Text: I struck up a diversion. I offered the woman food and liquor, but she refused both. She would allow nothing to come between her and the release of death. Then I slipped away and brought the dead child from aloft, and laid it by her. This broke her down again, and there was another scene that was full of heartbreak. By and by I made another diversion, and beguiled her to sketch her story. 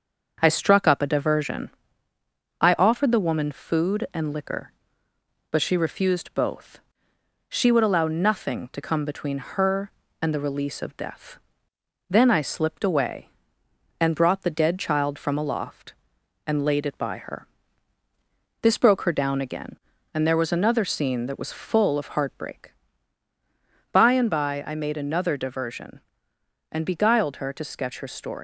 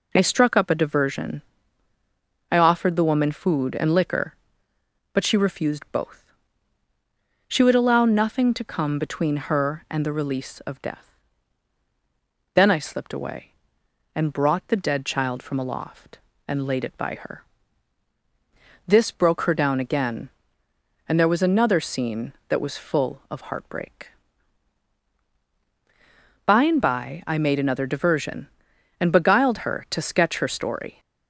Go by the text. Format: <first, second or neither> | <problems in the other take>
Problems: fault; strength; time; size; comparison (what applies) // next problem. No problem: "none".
second | starts louder than the rest; until 1.4 s; 6.5 dB // leaves "story" unfinished; at 28.3 s; 115 ms